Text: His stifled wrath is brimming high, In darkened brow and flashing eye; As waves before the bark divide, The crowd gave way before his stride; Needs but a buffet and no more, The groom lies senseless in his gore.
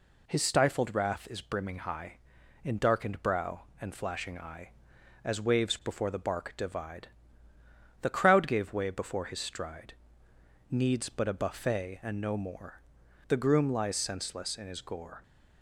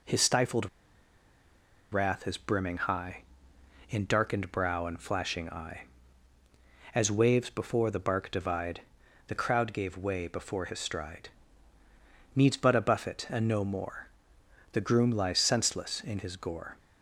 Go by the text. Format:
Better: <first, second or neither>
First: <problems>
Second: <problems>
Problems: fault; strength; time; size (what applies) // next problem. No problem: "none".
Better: first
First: none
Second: pauses between "stifled" and "wrath"; at 0.6 s; 1.2 s long